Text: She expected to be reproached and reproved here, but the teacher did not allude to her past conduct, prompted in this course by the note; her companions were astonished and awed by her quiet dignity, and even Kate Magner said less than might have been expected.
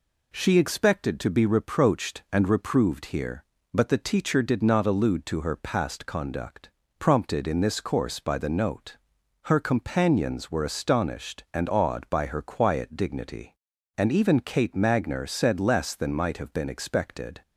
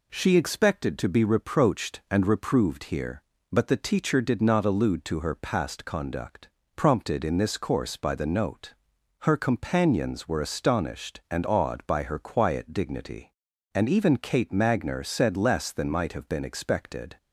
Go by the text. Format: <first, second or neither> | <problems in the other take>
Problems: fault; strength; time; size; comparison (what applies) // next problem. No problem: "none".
neither | none